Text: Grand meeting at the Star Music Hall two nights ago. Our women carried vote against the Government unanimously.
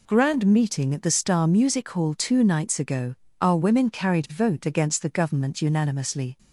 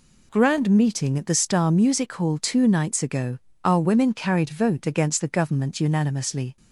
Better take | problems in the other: neither | none

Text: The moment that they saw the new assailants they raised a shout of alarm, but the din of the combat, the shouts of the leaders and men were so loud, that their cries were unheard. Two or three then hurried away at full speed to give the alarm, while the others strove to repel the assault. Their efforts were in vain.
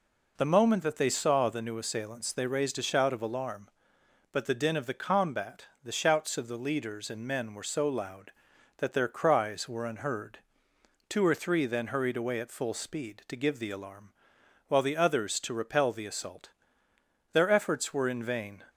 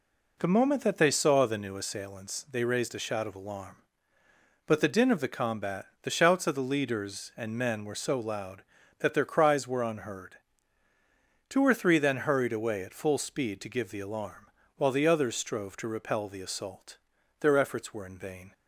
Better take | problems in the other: second | skips "strove"; at 15.3 s

